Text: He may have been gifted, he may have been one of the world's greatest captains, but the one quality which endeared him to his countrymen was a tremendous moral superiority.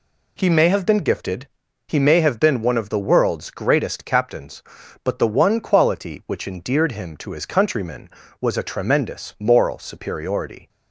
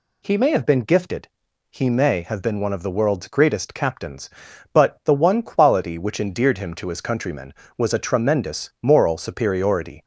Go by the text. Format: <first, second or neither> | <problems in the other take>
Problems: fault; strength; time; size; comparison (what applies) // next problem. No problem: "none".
neither | none